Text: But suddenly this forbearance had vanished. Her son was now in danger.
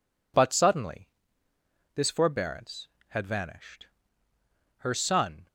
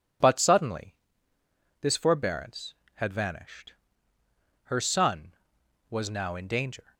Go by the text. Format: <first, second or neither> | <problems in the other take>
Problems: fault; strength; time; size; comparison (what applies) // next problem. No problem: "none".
second | pauses between "suddenly" and "this"; noticeable; at 1.0 s; 0.88 s long; noticeable in the second // stops before "was now in danger"; at 5.4 s